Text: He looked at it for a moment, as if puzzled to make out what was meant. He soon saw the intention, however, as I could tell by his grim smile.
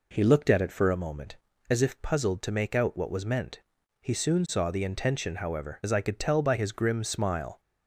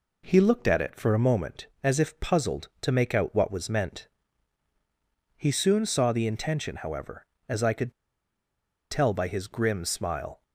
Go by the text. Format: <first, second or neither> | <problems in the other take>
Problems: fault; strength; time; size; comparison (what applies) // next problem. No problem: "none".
first | pauses between "could" and "tell"; at 7.9 s; 0.98 s long